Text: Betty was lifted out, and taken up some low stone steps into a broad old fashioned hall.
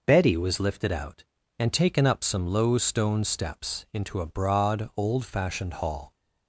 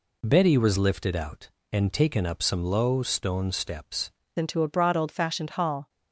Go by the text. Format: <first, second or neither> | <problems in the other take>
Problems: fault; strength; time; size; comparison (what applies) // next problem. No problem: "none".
first | changes voice at "into"; from 4.3 s on; 1.5 s long